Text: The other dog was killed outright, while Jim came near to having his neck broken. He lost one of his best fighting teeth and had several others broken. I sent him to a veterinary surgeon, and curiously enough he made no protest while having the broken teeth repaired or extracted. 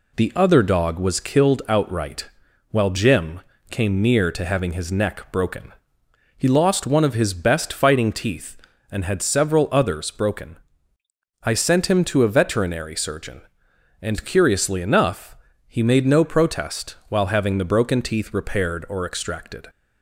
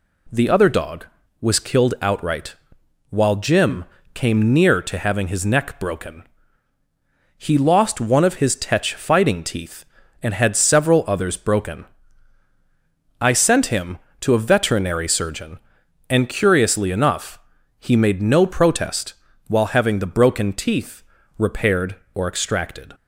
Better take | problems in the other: first | pauses between "Jim" and "came"; slight; at 3.8 s; 0.28 s long; slight in the first // says "tetch" for "best"; at 8.5 s // pauses between "enough" and "he"; at 17.3 s; 0.40 s long; slight in the first // pauses between "protest" and "while"; slight; at 19.1 s; 0.34 s long; slight in the first // pauses between "teeth" and "repaired"; slight; at 21.0 s; 0.34 s long

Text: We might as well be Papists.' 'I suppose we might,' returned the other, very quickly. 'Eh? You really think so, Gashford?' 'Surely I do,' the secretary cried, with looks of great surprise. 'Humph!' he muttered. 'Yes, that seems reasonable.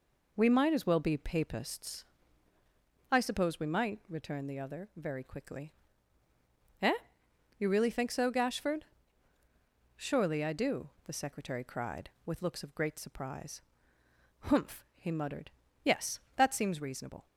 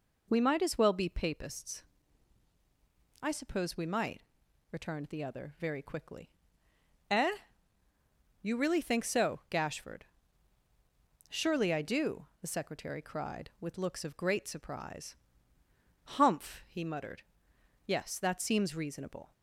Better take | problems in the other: neither | none

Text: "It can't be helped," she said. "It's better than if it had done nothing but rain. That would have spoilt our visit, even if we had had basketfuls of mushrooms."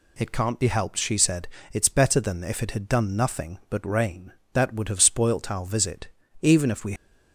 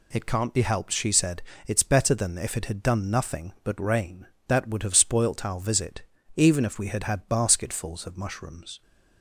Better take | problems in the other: second | stops before "had had basketfuls of mushrooms"; at 6.9 s

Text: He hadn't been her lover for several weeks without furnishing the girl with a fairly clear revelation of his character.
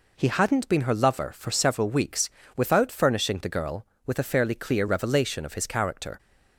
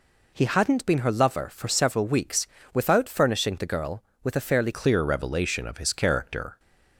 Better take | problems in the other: first | pauses between "weeks" and "without"; slight; at 2.4 s; 0.26 s long; slight in the first // changes voice at "clear"; from 4.7 s on; 1.8 s long

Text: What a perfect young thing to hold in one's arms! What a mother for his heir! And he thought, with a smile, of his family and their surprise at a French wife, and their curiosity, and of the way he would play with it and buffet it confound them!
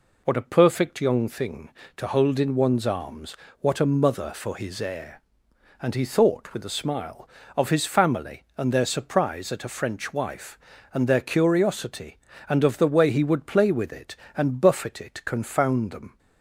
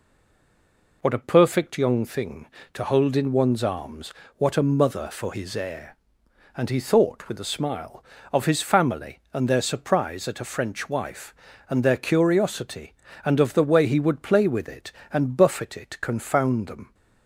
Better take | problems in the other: first | stays silent before the first word; until 1.0 s; 1.0 s long

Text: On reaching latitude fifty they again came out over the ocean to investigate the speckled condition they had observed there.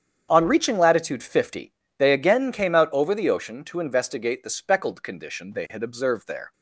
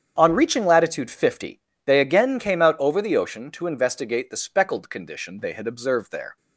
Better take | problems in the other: neither | starts louder than the rest; strong; the same in both // pauses between "fifty" and "they"; slight; the same in both

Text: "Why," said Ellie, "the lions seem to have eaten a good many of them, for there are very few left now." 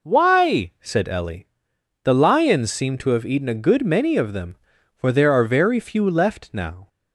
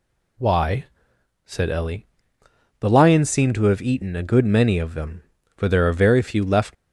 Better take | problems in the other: first | stops before "now"; at 6.7 s

